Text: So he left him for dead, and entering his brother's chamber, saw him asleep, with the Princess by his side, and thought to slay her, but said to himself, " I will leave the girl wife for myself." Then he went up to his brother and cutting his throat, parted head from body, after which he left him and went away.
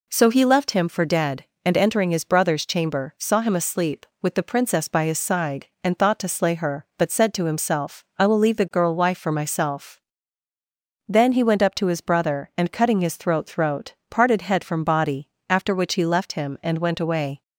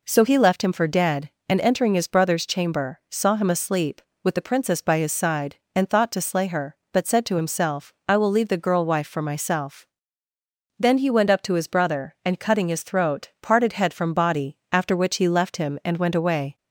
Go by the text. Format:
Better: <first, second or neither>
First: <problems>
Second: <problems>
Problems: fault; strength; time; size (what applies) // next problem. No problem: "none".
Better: second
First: says "throat" twice; at 13.4 s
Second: none